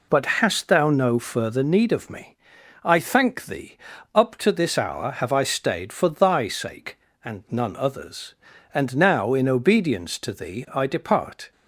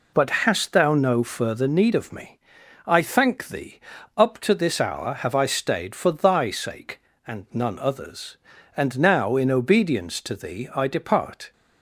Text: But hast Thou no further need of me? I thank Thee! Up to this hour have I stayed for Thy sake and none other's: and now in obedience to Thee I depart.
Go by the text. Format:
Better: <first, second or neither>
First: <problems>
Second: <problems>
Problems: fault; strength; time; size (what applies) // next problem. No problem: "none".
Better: neither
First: none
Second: none